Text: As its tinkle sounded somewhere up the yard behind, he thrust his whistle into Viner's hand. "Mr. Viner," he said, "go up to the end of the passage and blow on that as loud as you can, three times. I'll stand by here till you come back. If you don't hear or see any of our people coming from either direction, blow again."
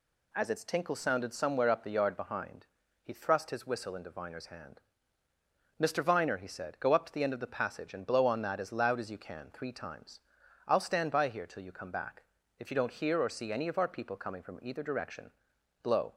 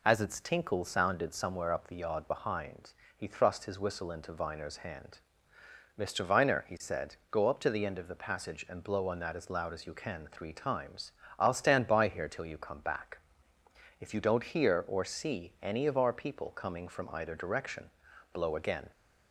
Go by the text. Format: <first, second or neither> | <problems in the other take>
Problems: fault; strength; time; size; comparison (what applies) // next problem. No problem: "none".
second | stops before "again"; at 16.1 s